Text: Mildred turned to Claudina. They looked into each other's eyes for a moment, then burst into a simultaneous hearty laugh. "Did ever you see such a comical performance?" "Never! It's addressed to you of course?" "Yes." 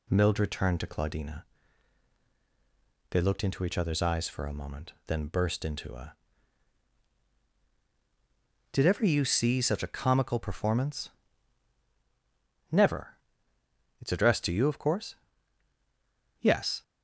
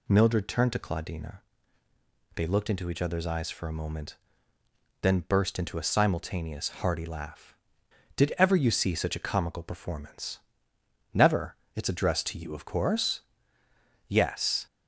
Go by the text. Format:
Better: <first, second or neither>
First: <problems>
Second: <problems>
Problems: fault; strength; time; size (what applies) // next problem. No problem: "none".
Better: second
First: skips "simultaneous hearty laugh"; at 7.4 s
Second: none